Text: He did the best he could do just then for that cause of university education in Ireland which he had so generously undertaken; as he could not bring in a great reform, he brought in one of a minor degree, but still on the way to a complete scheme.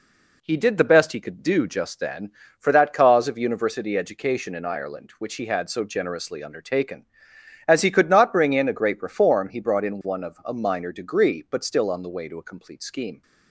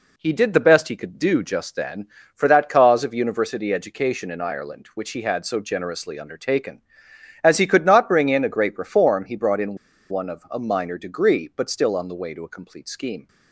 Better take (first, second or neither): first